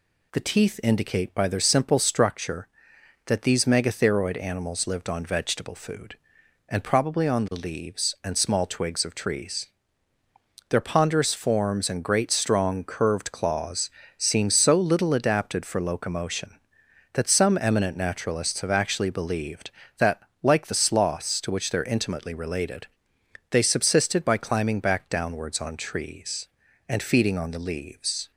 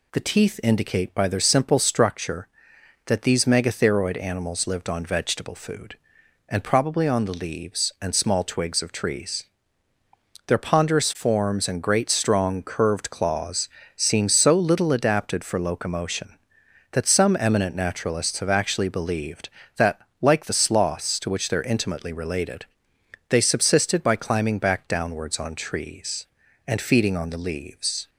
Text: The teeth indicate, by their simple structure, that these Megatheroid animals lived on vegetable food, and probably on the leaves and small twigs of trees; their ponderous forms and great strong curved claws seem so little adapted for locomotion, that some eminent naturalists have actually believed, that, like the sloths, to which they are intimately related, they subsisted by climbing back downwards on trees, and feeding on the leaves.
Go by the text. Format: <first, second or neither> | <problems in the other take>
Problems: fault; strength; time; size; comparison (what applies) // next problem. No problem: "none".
neither | pauses between "claws" and "seem"; slight; the same in both